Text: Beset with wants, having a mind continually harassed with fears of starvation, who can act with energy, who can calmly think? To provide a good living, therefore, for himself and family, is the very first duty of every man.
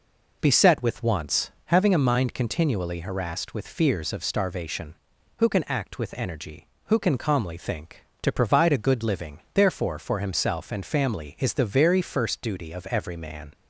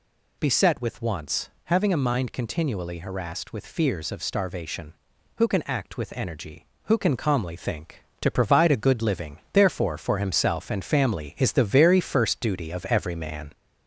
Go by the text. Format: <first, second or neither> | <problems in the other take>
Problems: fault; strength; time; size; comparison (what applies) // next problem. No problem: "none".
first | gets louder; slight; throughout; 3 dB